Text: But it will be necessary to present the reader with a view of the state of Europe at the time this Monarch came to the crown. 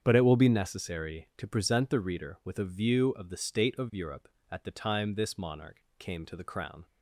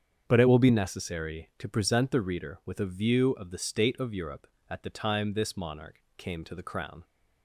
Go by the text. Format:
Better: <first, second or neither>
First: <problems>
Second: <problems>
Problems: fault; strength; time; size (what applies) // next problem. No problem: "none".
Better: neither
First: starts louder than the rest; strong; until 1.0 s; 8 dB // pauses between "Monarch" and "came"; slight; at 5.8 s; 0.18 s long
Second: starts louder than the rest; strong; until 1.2 s; 7.5 dB // pauses between "Monarch" and "came"; slight; at 5.9 s; 0.18 s long